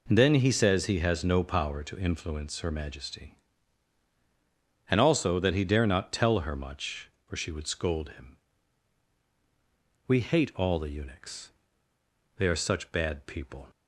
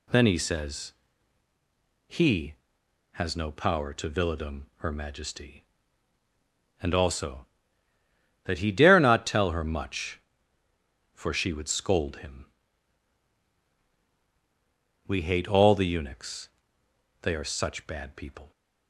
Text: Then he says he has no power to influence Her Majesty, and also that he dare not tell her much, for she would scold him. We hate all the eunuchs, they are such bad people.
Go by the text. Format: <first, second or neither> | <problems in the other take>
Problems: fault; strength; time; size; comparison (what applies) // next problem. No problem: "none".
first | pauses between "says" and "he"; at 0.9 s; 1.1 s long // says "villadom" for "influence"; at 4.0 s